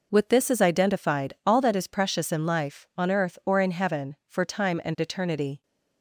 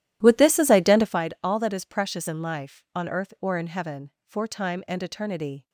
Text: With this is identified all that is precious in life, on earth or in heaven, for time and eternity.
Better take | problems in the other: first | starts louder than the rest; strong; until 1.2 s; 12.5 dB

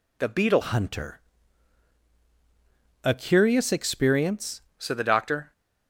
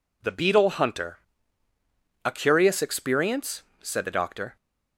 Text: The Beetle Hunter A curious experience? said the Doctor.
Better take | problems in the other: second | changes voice from "Hunter" to "experience"; from 0.6 to 4.6 s; 4.0 s long // pauses between "Hunter" and "A"; strong; at 1.1 s; 1.8 s long; also in the second

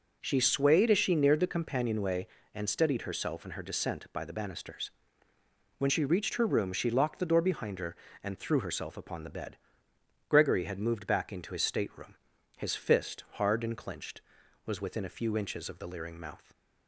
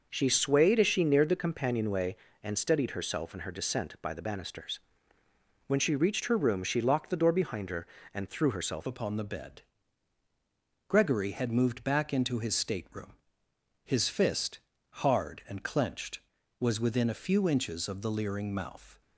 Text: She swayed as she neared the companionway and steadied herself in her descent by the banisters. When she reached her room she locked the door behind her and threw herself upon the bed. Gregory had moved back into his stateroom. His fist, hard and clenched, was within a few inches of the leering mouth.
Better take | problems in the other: first | changes voice at "upon"; from 8.8 s on; 10.2 s long

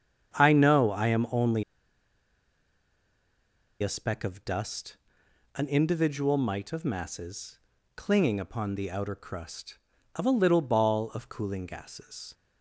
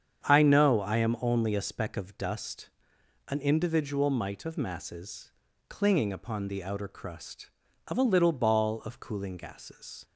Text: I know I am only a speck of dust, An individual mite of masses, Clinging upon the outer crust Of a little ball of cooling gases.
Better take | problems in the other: second | starts louder than the rest; strong; until 1.3 s; 8 dB; strong in the second // pauses between "only" and "a"; strong; at 1.6 s; 2.2 s long

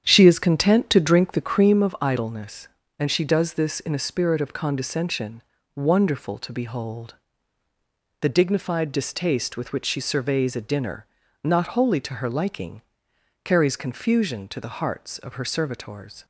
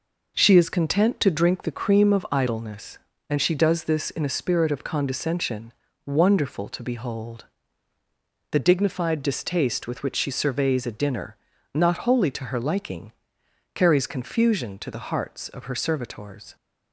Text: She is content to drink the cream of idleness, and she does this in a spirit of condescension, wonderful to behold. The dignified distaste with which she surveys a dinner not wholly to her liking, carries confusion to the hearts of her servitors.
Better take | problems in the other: second | starts louder than the rest; strong; until 1.8 s; 9 dB // pauses between "dinner" and "not"; slight; at 11.0 s; 0.36 s long; slight in the second

